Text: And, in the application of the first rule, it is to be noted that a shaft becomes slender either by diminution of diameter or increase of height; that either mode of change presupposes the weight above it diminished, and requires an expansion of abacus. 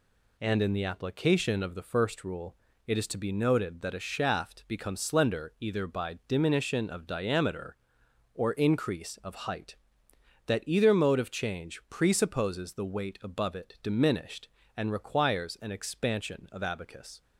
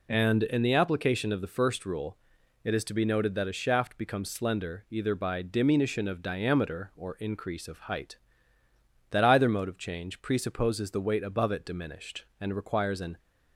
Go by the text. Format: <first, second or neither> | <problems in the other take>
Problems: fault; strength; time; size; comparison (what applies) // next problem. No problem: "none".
first | stops before "expansion of abacus"; at 13.1 s